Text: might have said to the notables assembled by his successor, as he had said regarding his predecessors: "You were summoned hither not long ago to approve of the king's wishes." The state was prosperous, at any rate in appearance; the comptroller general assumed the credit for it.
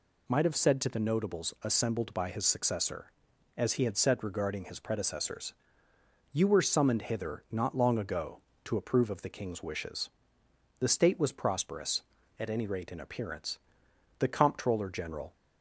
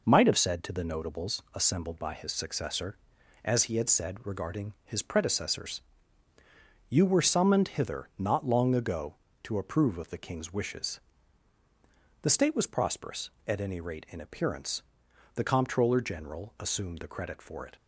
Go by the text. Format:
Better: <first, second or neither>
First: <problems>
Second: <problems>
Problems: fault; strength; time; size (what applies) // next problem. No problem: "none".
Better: second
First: stops before "assumed the credit for it"; at 15.3 s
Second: none